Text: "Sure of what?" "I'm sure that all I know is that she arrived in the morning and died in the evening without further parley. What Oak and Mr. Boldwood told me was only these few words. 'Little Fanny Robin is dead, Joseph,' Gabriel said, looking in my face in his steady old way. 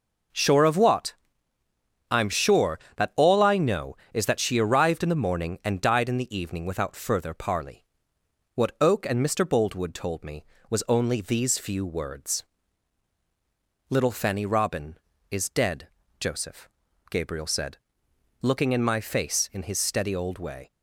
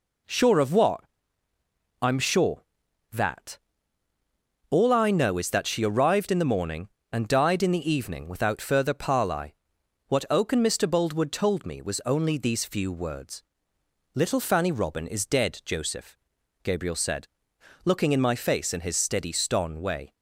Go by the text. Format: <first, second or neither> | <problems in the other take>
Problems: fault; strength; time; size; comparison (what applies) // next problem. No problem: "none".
first | pauses between "that" and "all"; at 3.5 s; 1.1 s long // says "ston" for "old"; at 19.3 s